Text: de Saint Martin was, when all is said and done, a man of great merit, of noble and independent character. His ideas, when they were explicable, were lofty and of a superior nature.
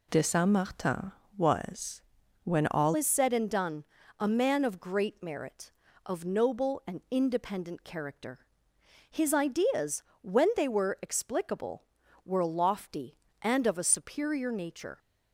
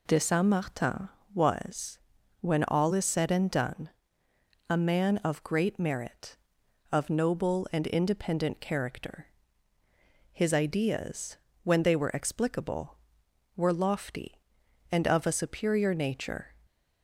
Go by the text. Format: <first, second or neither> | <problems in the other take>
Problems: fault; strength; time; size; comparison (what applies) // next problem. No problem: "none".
second | changes voice at "is"; from 2.9 s on; 12.0 s long